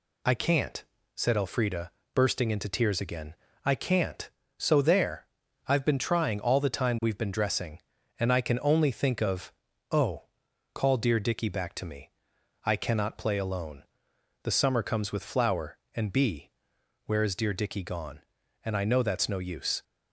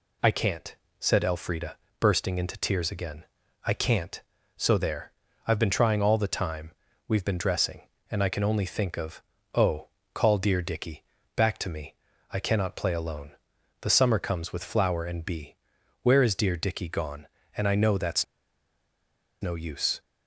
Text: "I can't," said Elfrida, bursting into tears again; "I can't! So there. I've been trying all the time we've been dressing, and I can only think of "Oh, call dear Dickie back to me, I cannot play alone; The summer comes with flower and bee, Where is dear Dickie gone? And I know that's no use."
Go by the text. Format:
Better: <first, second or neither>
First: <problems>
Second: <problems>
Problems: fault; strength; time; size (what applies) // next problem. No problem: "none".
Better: first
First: pauses between "of" and "Oh"; at 9.5 s; 0.38 s long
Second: pauses between "time" and "we've"; slight; at 6.7 s; 0.34 s long // pauses between "of" and "Oh"; slight; at 9.2 s; 0.32 s long // pauses between "Dickie" and "back"; slight; at 11.0 s; 0.30 s long // pauses between "that's" and "no"; at 18.2 s; 1.1 s long